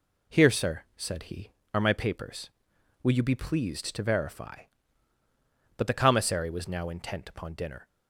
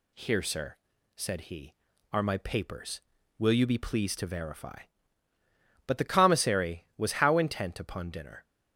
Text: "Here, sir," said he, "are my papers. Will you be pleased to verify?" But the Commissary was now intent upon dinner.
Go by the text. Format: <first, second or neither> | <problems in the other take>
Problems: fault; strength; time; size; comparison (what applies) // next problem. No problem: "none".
first | says "how" for "now"; at 7.1 s